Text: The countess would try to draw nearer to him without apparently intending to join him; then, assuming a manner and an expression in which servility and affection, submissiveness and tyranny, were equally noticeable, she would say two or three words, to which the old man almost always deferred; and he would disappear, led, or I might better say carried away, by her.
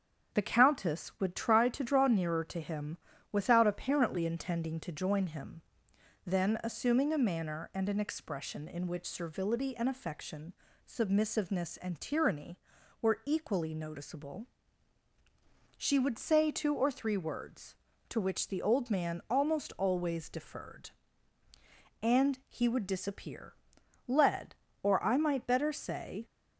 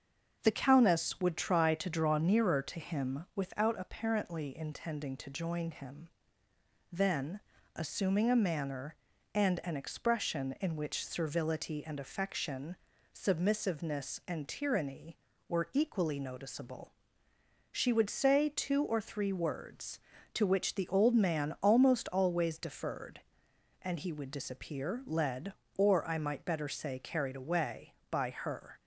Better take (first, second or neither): second